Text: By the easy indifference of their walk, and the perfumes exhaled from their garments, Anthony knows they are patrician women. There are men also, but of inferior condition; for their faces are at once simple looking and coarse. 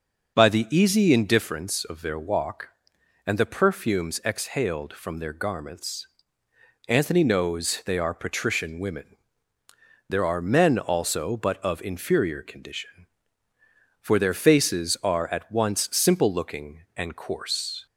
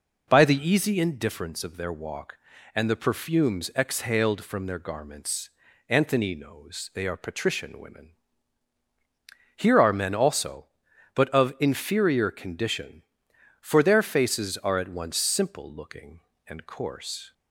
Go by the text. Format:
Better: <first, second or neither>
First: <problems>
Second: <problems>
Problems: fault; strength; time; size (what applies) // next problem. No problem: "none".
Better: first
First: none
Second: says "Here" for "There"; at 9.5 s